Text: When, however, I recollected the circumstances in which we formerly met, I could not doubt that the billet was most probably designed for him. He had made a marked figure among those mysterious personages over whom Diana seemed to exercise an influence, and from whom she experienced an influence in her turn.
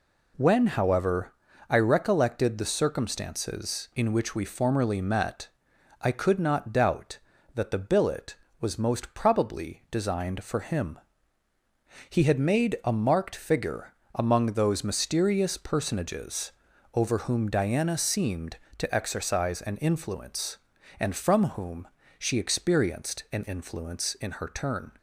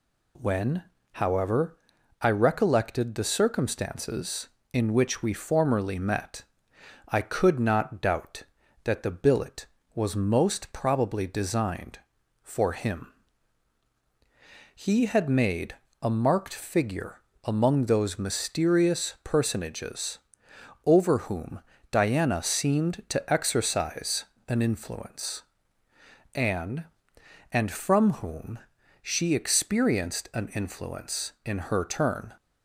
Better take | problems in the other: first | pauses between "made" and "a"; slight; at 15.7 s; 0.28 s long // pauses between "figure" and "among"; slight; at 17.2 s; 0.24 s long; slight in the first // pauses between "personages" and "over"; noticeable; at 20.1 s; 0.66 s long; also in the first // pauses between "whom" and "Diana"; slight; at 21.6 s; 0.30 s long // pauses between "exercise" and "an"; slight; at 24.2 s; 0.24 s long // says "and" twice; at 27.5 s // pauses between "whom" and "she"; at 28.5 s; 0.44 s long; slight in the first

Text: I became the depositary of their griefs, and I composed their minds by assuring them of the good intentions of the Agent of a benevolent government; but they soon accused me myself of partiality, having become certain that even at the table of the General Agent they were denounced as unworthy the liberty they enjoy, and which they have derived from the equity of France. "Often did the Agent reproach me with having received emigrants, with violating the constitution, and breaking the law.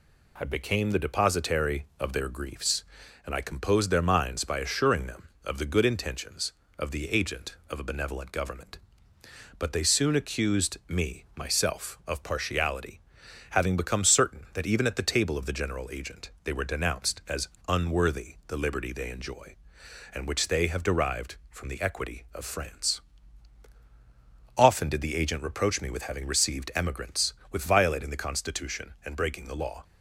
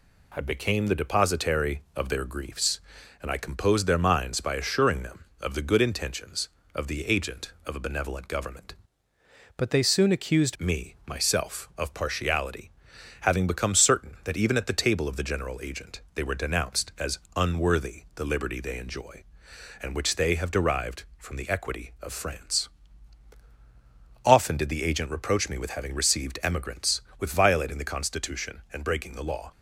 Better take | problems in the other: first | changes voice from "but" to "accused"; from 9.5 to 10.5 s; 1.0 s long // pauses between "Agent" and "they"; slight; at 15.9 s; 0.16 s long; slight in the first // pauses between "as" and "unworthy"; slight; at 17.1 s; 0.16 s long; slight in the first

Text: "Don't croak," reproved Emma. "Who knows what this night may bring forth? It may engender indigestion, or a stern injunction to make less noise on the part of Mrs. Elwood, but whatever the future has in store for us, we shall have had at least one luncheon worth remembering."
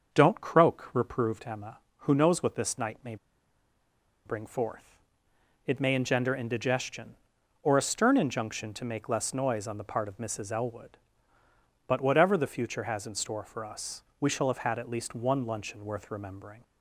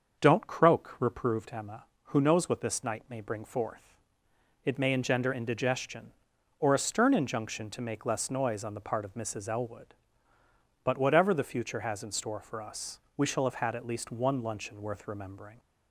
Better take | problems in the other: second | starts louder than the rest; until 1.1 s; 6.5 dB; also in the second // pauses between "may" and "bring"; at 3.1 s; 1.1 s long

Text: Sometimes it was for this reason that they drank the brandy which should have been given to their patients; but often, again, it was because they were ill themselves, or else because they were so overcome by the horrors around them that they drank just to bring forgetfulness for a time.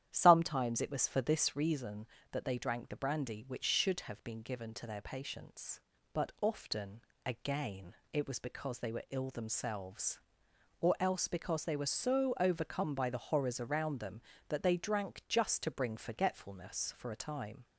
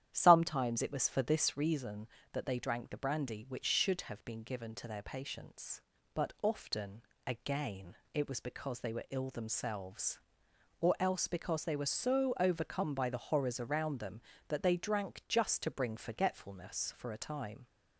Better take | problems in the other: neither | starts louder than the rest; strong; the same in both

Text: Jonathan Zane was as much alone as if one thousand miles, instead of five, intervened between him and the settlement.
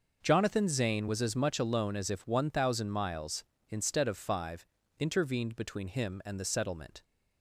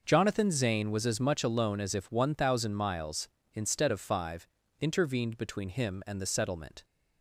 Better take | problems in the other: neither | none

